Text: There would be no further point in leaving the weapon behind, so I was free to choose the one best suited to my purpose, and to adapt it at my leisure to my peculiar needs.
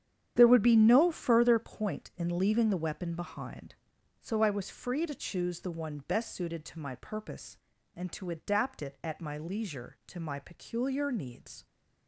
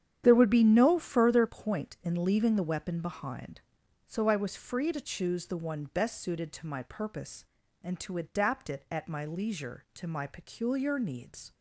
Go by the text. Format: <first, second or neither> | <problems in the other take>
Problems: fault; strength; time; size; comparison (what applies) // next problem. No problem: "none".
neither | starts louder than the rest; strong; the same in both